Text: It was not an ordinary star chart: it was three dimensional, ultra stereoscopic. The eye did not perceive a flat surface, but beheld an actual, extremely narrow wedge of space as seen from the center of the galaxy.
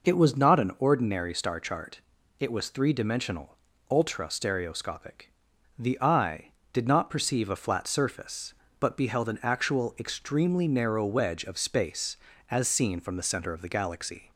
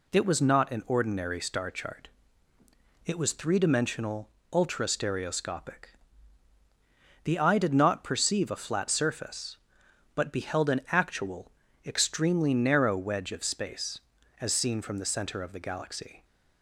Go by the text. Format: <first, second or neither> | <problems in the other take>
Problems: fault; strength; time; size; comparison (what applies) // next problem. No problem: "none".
neither | none